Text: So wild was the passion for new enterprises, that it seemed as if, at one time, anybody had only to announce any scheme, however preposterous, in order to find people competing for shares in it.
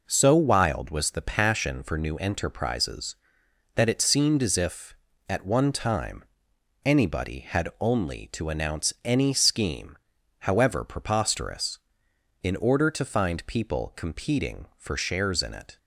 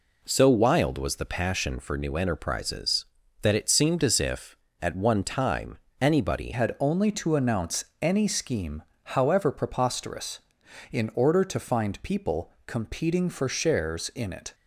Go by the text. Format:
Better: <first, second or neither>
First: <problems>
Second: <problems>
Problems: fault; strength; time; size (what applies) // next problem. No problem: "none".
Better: first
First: none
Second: changes voice at "had"; from 6.5 s on; 8.0 s long // pauses between "announce" and "any"; slight; at 7.8 s; 0.18 s long // pauses between "people" and "competing"; slight; at 12.5 s; 0.16 s long